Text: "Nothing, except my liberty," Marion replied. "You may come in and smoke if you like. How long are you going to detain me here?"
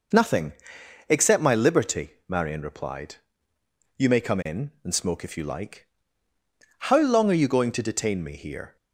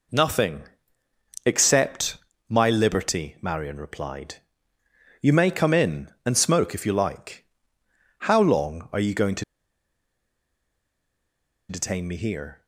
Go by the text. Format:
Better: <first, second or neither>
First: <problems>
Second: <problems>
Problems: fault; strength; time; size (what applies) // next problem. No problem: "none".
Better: first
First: none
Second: pauses between "except" and "my"; slight; at 2.1 s; 0.32 s long // pauses between "to" and "detain"; strong; at 9.4 s; 2.2 s long